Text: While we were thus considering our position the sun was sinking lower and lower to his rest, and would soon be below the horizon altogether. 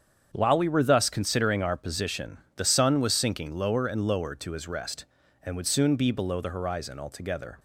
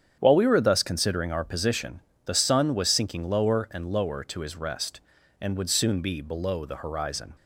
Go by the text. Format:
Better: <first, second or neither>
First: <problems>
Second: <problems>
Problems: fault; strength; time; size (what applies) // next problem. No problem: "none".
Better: first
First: starts louder than the rest; strong; until 1.3 s; 7.5 dB // pauses between "position" and "the"; slight; at 2.3 s; 0.18 s long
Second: starts louder than the rest; strong; until 1.1 s; 8 dB // pauses between "position" and "the"; slight; at 2.0 s; 0.24 s long // stops before "altogether"; at 7.3 s